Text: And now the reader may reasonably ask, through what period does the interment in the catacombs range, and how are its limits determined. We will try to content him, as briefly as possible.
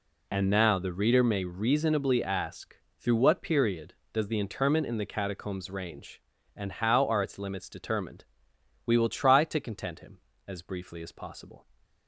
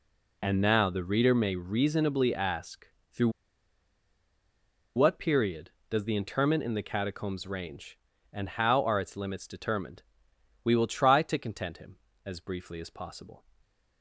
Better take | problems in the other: first | pauses between "through" and "what"; strong; at 3.2 s; 1.6 s long // stays silent after the last word; slight; from 13.5 s on; 0.5 s long

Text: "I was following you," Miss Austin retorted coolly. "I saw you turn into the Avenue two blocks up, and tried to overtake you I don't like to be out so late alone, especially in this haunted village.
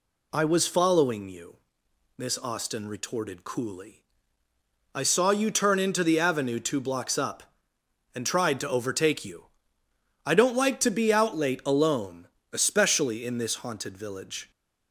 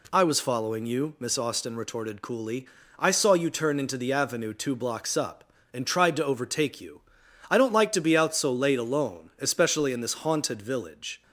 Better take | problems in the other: second | pauses between "you" and "I"; noticeable; at 9.4 s; 0.80 s long; noticeable in the second // skips "so"; at 11.3 s

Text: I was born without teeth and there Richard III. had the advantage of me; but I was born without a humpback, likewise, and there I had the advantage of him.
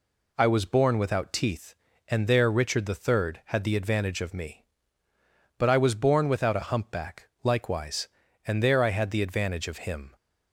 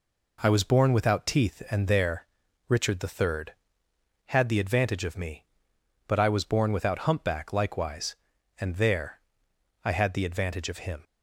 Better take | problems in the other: first | pauses between "there" and "Richard"; at 2.2 s; 0.44 s long // skips "a"; at 6.9 s // pauses between "there" and "I"; noticeable; at 9.1 s; 0.64 s long

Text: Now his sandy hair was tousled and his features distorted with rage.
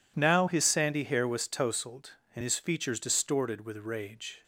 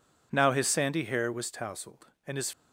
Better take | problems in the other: first | stops before "features distorted with rage"; at 2.5 s

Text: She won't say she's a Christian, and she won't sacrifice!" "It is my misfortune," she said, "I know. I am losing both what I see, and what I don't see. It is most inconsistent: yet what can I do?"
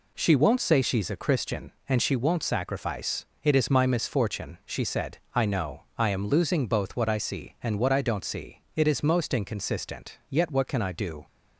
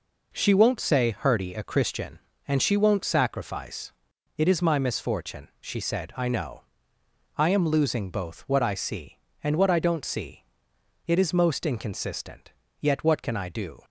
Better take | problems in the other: first | says "hurdy" for "she's"; at 1.1 s

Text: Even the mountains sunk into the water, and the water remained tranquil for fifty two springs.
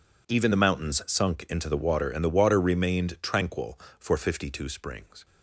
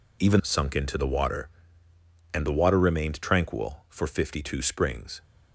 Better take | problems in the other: first | skips "the mountains"; at 0.4 s

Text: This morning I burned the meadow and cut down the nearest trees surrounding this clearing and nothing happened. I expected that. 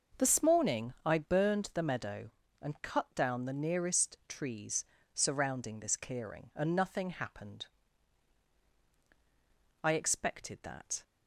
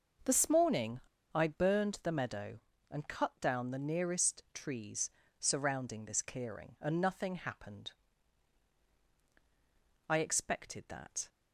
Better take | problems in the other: first | pauses between "morning" and "I"; slight; at 0.9 s; 0.32 s long // pauses between "trees" and "surrounding"; slight; at 5.0 s; 0.30 s long; slight in the first

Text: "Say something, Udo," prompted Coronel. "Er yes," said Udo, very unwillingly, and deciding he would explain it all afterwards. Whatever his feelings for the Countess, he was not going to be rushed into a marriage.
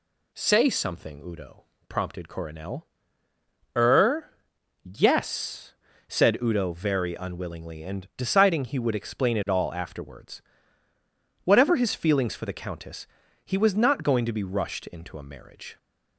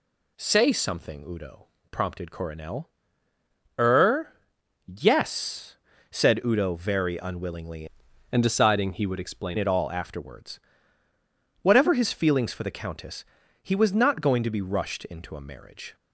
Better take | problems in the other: first | pauses between "Er" and "yes"; noticeable; at 4.3 s; 0.52 s long; noticeable in the first // changes voice from "and" to "explain"; from 8.3 to 9.5 s; 1.2 s long

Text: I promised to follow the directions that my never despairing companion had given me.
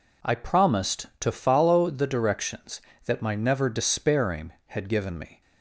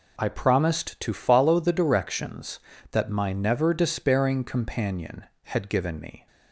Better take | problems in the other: second | skips "companion"; at 4.5 s

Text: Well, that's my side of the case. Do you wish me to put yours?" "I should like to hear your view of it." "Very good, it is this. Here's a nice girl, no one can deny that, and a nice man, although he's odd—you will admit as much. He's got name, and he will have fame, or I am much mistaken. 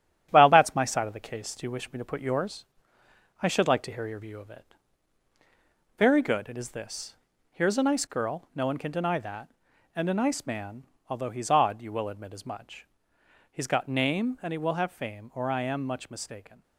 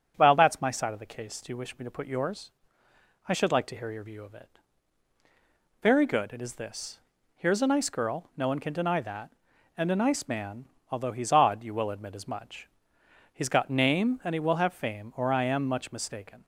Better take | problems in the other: second | gets quieter; noticeable; throughout; 4.5 dB // starts louder than the rest; strong; until 1.3 s; 11 dB; strong in the second

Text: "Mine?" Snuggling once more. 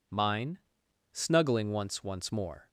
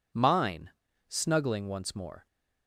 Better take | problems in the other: second | says "once" twice; at 2.0 s

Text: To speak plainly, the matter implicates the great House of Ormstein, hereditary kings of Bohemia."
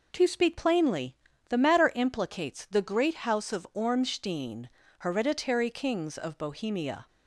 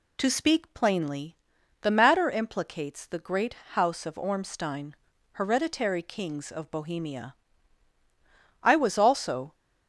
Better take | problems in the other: first | pauses between "great" and "House"; slight; at 3.5 s; 0.18 s long // goes on to say "I was also"; noticeable; from 8.6 s on; 0.92 s long

